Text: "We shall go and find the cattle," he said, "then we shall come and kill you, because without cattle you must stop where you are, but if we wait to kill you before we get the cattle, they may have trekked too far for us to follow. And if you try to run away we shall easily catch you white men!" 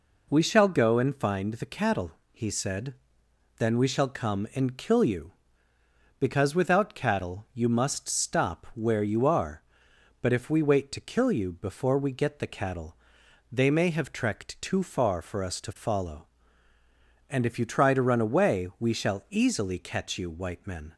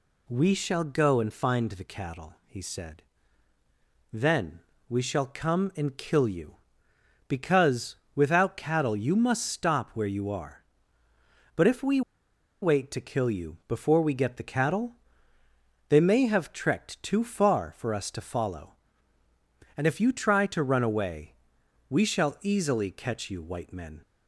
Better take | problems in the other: first | pauses between "then" and "we"; slight; at 4.6 s; 0.28 s long // pauses between "because" and "without"; slight; at 7.9 s; 0.18 s long // pauses between "we" and "wait"; noticeable; at 12.0 s; 0.61 s long // pauses between "away" and "we"; noticeable; at 21.3 s; 0.54 s long

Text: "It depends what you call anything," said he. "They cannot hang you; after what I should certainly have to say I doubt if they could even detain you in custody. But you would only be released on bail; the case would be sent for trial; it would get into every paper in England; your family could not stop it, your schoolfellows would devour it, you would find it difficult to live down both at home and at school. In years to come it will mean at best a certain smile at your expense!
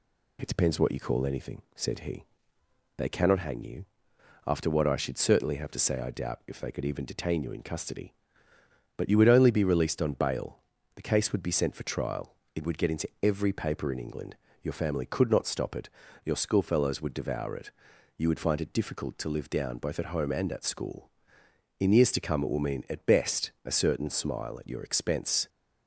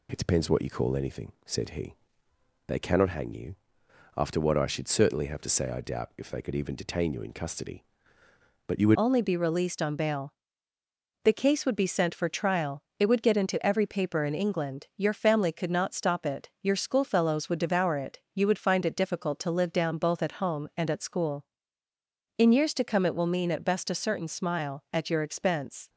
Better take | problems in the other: first | changes voice at "only"; from 8.9 s on; 16.9 s long

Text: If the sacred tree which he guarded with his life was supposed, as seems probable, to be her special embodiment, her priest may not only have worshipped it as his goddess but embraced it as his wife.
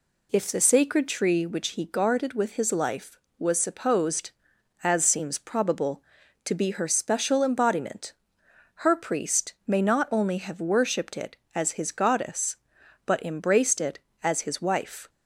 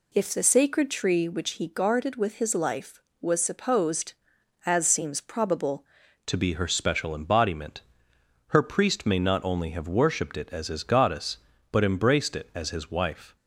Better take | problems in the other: first | changes voice at "to"; from 6.2 s on; 7.1 s long

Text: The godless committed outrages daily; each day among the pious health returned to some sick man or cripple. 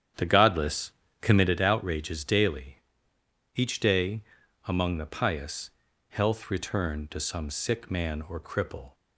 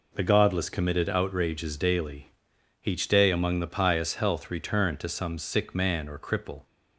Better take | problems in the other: second | starts louder than the rest; strong; until 1.5 s; 9 dB // pauses between "godless" and "committed"; slight; at 0.9 s; 0.30 s long // pauses between "day" and "among"; at 4.2 s; 0.44 s long // pauses between "pious" and "health"; at 5.6 s; 0.40 s long

